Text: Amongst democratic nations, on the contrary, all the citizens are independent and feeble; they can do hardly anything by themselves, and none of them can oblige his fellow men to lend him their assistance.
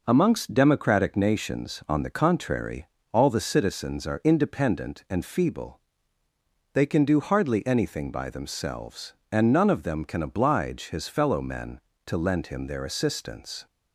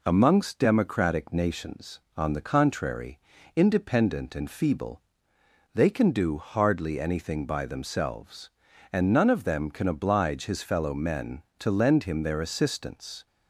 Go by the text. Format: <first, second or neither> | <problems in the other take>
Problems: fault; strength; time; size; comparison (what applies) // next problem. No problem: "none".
first | skips "all the citizens are"; at 3.3 s